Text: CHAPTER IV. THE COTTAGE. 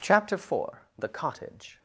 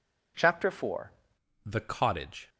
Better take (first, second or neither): first